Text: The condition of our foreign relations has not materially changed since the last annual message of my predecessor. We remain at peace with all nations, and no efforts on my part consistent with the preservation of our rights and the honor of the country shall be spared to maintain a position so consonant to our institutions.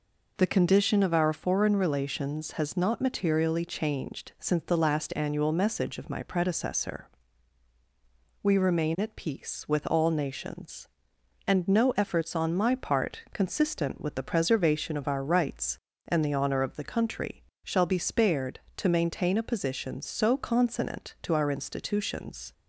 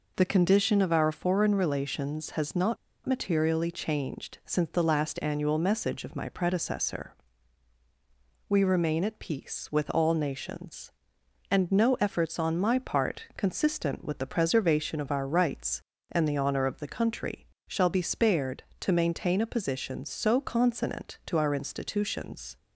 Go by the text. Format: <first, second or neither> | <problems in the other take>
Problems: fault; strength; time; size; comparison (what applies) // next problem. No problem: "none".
first | pauses between "not" and "materially"; slight; at 2.7 s; 0.29 s long // pauses between "country" and "shall"; slight; at 17.4 s; 0.22 s long; slight in the first